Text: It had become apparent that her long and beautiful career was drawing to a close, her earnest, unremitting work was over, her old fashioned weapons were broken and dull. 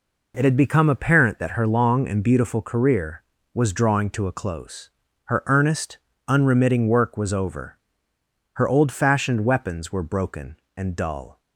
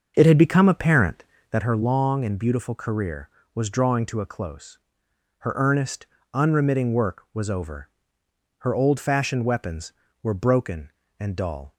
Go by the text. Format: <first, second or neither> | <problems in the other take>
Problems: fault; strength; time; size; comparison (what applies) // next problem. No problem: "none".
first | starts louder than the rest; until 1.6 s; 6.5 dB